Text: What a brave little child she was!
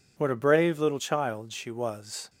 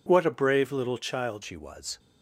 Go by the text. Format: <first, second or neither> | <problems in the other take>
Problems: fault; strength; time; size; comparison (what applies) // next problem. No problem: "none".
first | changes voice at "she"; from 1.4 s on; 0.5 s long